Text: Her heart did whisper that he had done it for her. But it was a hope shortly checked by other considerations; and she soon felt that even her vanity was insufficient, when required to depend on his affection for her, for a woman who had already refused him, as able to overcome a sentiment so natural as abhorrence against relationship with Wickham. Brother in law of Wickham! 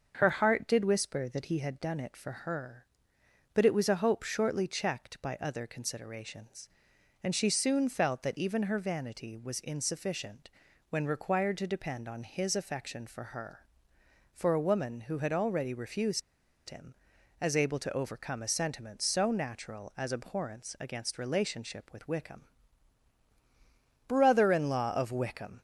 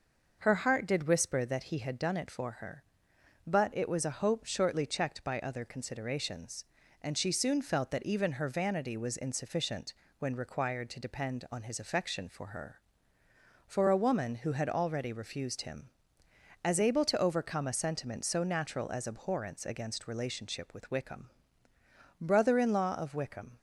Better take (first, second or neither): second